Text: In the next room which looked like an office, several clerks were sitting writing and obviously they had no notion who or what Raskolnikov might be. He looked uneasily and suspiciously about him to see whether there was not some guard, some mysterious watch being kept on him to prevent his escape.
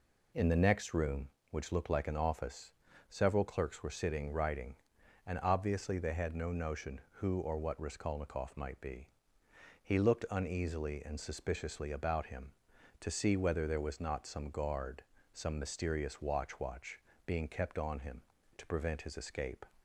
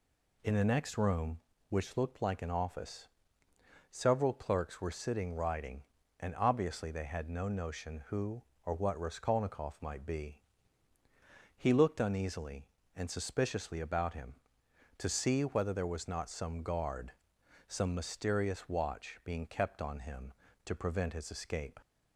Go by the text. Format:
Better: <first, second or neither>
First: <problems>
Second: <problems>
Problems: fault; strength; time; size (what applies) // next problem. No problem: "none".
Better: second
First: says "watch" twice; at 16.5 s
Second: none